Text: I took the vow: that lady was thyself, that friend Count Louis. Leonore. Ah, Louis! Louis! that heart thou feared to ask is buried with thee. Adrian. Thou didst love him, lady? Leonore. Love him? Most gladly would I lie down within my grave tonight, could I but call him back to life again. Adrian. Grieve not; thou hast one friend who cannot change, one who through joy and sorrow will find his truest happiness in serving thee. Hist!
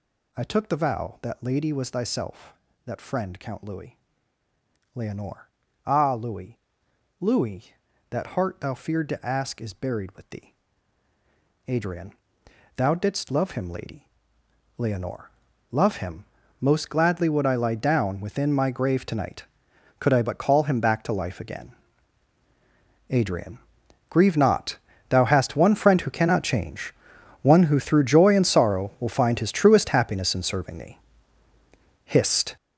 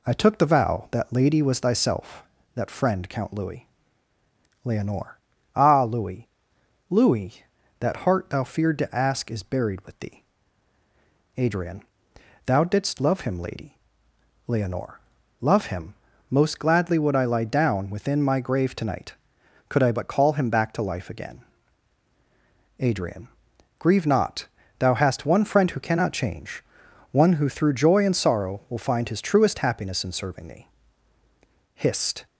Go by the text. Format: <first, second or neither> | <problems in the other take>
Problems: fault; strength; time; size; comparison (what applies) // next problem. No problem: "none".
second | gets louder; strong; throughout; 12 dB